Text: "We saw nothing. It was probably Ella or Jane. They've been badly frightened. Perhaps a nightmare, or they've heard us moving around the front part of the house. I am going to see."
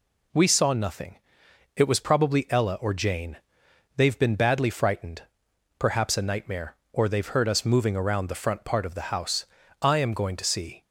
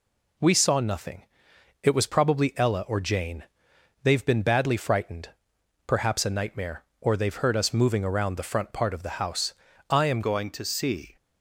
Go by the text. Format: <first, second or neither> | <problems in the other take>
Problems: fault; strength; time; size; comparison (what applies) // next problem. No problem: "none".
first | changes voice at "going"; from 10.2 s on; 0.9 s long